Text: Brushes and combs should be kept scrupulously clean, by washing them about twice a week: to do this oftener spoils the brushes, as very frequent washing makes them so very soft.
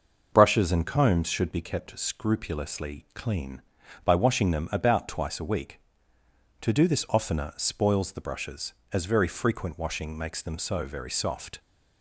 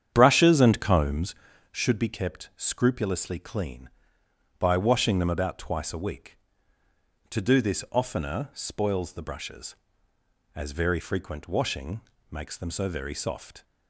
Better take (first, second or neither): first